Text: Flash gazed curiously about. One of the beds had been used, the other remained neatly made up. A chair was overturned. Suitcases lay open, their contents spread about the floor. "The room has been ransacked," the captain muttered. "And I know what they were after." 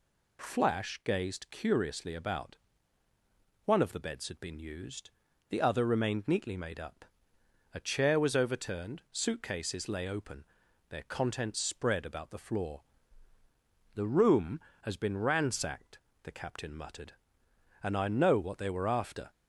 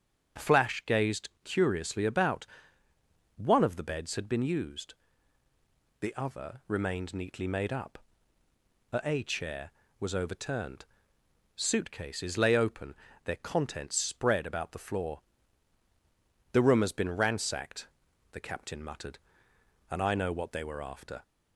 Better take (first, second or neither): first